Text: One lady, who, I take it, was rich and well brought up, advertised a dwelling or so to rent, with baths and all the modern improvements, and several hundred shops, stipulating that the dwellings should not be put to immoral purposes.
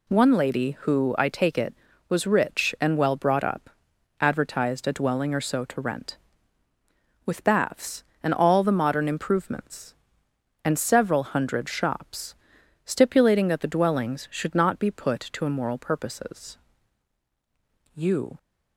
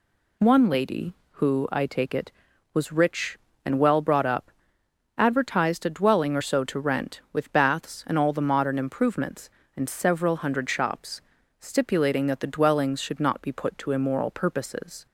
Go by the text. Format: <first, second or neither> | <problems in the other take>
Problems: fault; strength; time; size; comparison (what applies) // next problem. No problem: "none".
second | goes on to say "You"; slight; from 17.9 s on; 0.42 s long